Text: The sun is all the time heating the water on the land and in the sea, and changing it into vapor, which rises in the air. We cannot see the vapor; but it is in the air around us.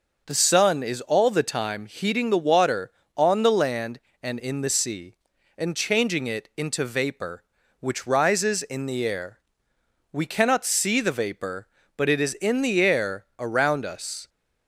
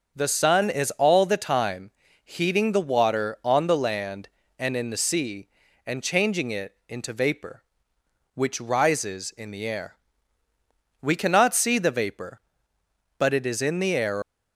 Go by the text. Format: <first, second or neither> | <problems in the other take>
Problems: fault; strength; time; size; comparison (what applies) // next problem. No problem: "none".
first | starts louder than the rest; until 1.2 s; 6.5 dB // pauses between "time" and "heating"; slight; at 1.9 s; 0.32 s long // stops before "around us"; at 14.2 s